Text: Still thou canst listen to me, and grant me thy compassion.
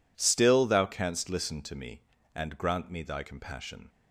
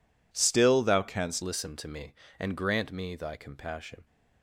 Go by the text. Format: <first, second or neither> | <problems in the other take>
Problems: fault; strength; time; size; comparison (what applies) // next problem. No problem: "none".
first | changes voice at "listen"; from 1.4 s on; 2.6 s long